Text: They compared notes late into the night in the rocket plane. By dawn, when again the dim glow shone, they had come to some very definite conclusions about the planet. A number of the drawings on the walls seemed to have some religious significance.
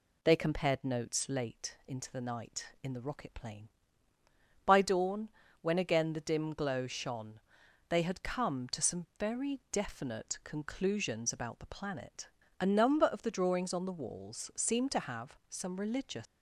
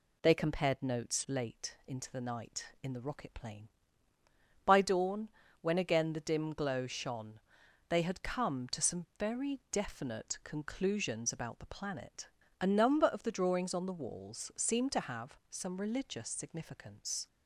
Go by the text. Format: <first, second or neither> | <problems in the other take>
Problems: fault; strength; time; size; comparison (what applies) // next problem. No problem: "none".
second | stops before "significance"; at 16.2 s